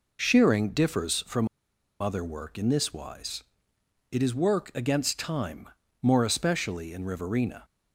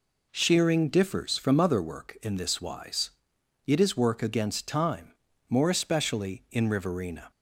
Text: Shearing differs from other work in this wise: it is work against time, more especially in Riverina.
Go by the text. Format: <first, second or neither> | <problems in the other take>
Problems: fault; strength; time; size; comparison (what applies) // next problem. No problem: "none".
second | pauses between "from" and "other"; noticeable; at 1.4 s; 0.53 s long